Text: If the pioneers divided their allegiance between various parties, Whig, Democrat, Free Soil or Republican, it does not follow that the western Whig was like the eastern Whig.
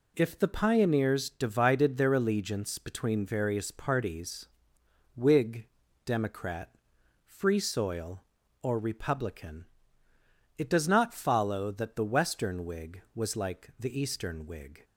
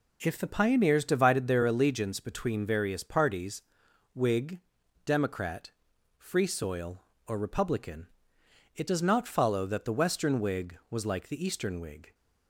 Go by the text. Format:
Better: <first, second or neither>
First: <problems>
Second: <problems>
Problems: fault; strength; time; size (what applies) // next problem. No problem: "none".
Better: neither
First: none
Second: none